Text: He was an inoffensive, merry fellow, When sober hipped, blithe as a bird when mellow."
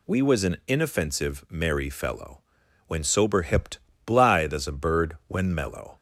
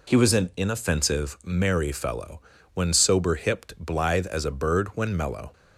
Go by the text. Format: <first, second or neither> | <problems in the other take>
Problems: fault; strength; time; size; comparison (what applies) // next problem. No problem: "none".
second | says "We" for "He"; at 0.0 s